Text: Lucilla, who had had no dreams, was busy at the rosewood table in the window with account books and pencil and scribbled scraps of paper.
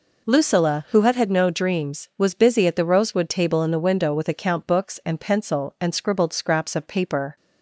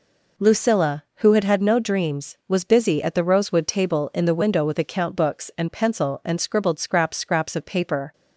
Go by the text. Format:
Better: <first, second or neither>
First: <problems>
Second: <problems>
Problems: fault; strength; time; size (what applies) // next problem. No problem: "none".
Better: first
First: none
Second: says "scraps" twice; at 7.1 s